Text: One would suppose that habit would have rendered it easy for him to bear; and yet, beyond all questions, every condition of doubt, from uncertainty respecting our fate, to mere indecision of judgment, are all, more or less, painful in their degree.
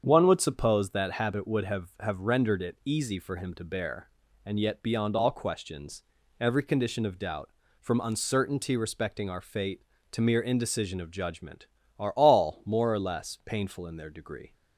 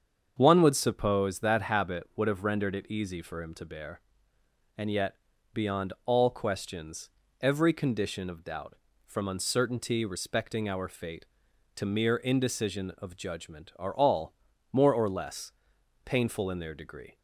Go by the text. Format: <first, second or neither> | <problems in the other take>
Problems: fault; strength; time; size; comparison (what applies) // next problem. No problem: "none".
second | starts louder than the rest; strong; until 1.0 s; 7.5 dB; strong in the second // says "have" twice; at 1.9 s